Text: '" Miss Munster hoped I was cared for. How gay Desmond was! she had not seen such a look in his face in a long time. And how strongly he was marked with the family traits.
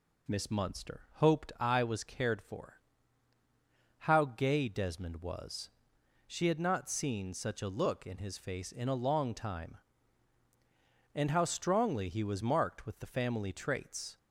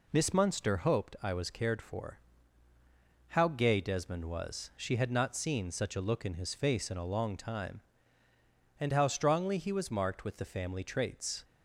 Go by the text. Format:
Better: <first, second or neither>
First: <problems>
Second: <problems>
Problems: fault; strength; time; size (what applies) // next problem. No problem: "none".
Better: neither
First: none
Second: none